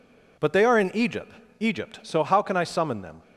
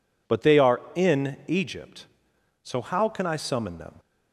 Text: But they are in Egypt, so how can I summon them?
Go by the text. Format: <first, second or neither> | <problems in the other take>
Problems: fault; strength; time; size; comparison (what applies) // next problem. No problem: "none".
second | says "Egypt" twice; at 1.5 s